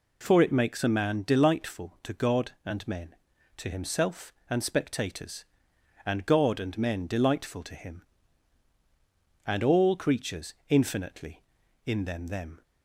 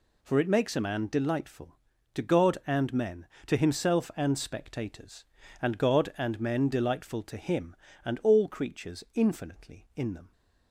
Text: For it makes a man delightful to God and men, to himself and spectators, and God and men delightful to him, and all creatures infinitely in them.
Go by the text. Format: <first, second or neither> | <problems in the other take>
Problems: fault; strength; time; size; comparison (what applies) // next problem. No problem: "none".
second | pauses between "creatures" and "infinitely"; slight; at 10.5 s; 0.16 s long // says "them" twice; at 12.2 s